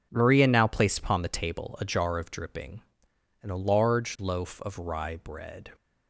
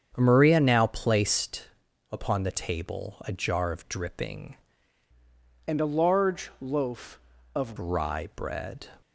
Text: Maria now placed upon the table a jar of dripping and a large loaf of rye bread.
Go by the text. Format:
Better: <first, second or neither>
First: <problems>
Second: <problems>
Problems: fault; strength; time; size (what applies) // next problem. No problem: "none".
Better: first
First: none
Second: starts louder than the rest; strong; until 1.1 s; 7.5 dB // pauses between "placed" and "upon"; at 1.6 s; 0.42 s long // changes voice from "and" to "of"; from 5.6 to 7.7 s; 2.1 s long